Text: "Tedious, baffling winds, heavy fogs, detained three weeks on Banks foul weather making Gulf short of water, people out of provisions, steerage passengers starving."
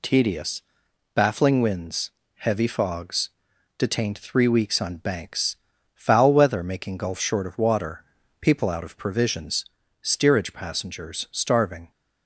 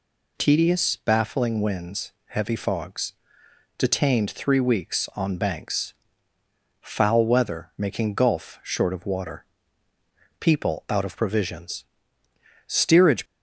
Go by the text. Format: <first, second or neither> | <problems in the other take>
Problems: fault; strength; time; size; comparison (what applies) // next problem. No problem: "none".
first | pauses between "Banks" and "foul"; noticeable; at 5.9 s; 0.88 s long; also in the first // stops before "passengers starving"; at 13.2 s